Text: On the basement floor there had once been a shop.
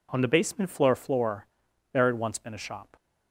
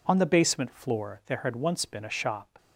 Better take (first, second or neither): second